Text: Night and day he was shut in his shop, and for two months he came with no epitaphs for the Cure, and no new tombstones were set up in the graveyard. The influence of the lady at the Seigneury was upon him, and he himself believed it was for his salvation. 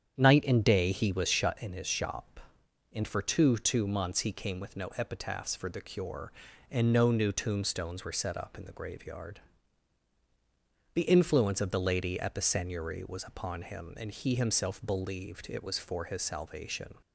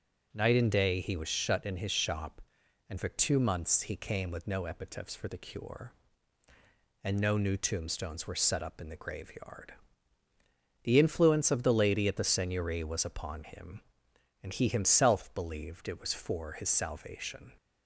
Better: second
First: starts louder than the rest; strong; until 1.2 s; 8.5 dB // says "two" twice; at 3.5 s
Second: none

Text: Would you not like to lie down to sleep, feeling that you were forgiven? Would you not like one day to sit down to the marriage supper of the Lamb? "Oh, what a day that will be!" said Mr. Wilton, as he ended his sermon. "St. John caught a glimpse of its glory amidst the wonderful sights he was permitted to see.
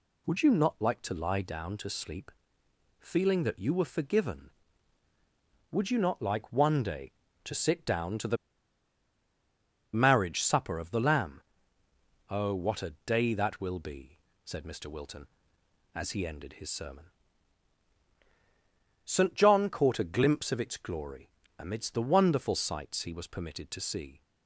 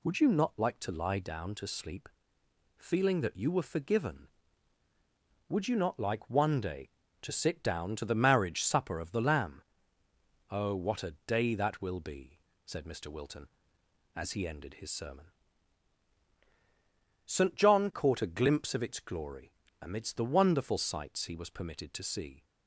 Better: second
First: pauses between "the" and "marriage"; strong; at 8.3 s; 1.5 s long // pauses between "glory" and "amidst"; slight; at 21.2 s; 0.28 s long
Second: pauses between "glory" and "amidst"; slight; at 19.5 s; 0.28 s long

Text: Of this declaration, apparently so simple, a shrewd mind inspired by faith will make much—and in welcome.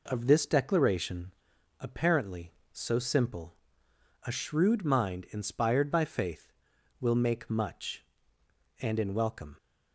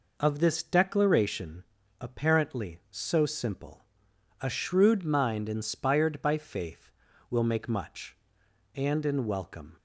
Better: neither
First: none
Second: none

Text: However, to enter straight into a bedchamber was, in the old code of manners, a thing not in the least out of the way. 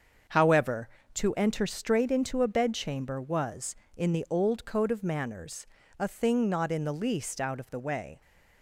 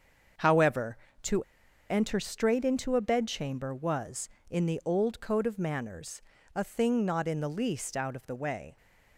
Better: first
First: starts louder than the rest; until 1.5 s; 7 dB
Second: starts louder than the rest; until 2.1 s; 7 dB // pauses between "to" and "enter"; noticeable; at 1.4 s; 0.47 s long

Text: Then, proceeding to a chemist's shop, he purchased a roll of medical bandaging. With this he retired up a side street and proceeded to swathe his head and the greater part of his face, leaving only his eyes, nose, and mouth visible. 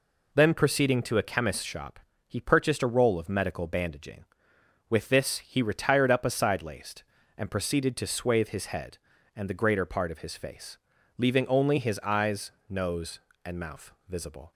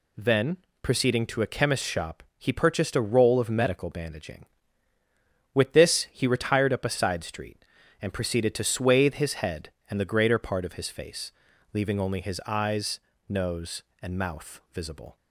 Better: second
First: says "laced" for "street"; at 6.6 s // pauses between "mouth" and "visible"; slight; at 13.9 s; 0.16 s long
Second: none

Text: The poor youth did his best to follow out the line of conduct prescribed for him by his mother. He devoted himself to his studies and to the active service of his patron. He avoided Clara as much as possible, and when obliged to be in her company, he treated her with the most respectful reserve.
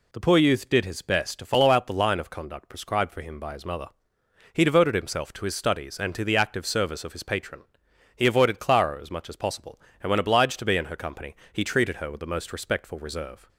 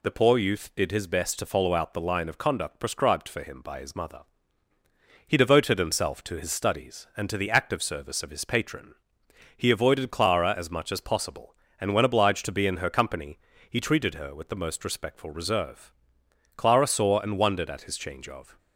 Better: first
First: none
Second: goes on to say "Clara saw and wondered at his change of"; strong; from 16.5 s on; 2.0 s long

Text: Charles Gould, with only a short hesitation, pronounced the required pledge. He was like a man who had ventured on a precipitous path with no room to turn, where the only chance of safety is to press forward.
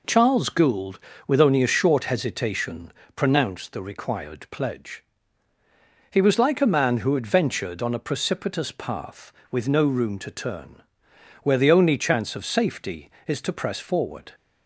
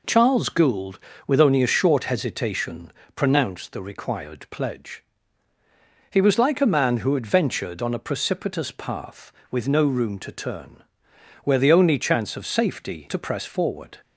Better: first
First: none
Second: skips "is"; at 13.0 s

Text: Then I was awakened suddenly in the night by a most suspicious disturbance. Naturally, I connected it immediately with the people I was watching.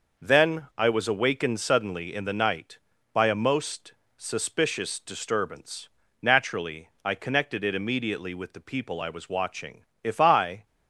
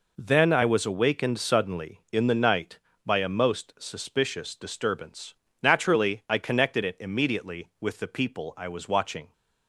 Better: second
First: pauses between "most" and "suspicious"; slight; at 3.9 s; 0.24 s long // goes on to say "If I"; noticeable; from 10.0 s on; 0.62 s long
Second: none

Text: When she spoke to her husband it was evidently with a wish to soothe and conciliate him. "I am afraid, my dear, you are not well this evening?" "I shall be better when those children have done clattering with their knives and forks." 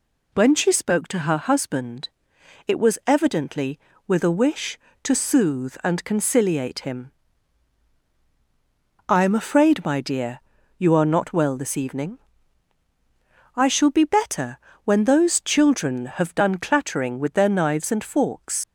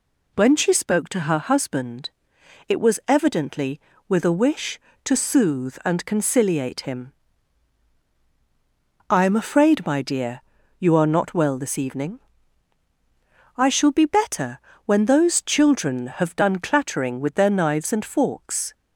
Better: second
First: pauses between "husband" and "it"; noticeable; at 2.0 s; 0.58 s long // pauses between "better" and "when"; slight; at 14.5 s; 0.28 s long // leaves "forks" unfinished; at 18.6 s; 80 ms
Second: pauses between "husband" and "it"; noticeable; at 2.0 s; 0.58 s long // pauses between "better" and "when"; slight; at 14.5 s; 0.28 s long

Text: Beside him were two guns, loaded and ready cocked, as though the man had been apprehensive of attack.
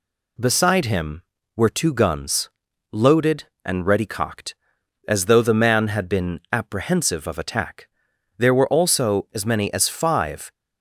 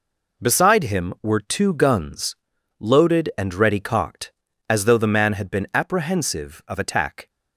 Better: second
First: goes on to say "There were also as many as five"; strong; from 8.3 s on; 2.1 s long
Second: none

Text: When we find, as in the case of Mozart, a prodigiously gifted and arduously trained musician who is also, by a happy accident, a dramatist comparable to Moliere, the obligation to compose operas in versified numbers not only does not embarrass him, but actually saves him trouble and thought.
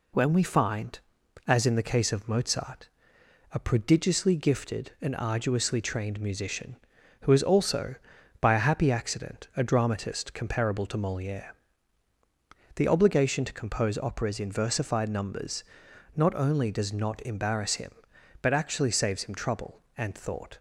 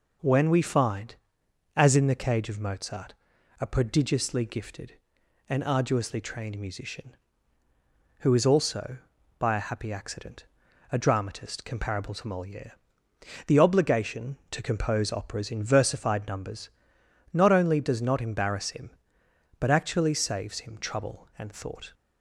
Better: first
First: pauses between "numbers" and "not"; noticeable; at 15.6 s; 0.50 s long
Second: says "cage" for "case"; at 2.1 s // pauses between "numbers" and "not"; noticeable; at 16.6 s; 0.62 s long

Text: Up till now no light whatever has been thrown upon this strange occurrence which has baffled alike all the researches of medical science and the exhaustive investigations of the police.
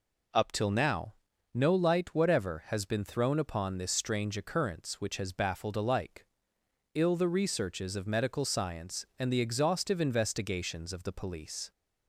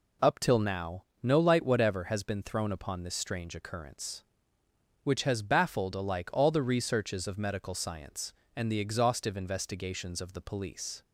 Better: second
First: pauses between "now" and "no"; at 1.1 s; 0.42 s long // says "ill" for "all"; at 6.9 s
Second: pauses between "now" and "no"; slight; at 1.0 s; 0.18 s long

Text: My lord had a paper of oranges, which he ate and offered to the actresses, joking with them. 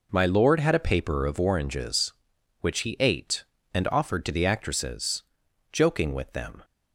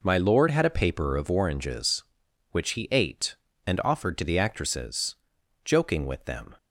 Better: neither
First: none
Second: none

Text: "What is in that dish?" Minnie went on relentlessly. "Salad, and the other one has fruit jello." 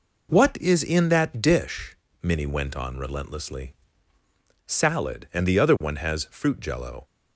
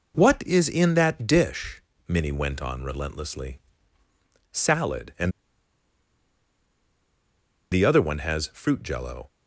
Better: first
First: none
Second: pauses between "and" and "the"; strong; at 5.2 s; 2.4 s long

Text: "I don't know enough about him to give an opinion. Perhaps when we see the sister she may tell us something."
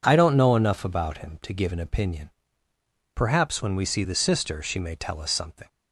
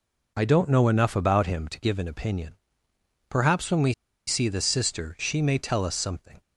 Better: first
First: none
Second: pauses between "we" and "see"; slight; at 3.9 s; 0.33 s long

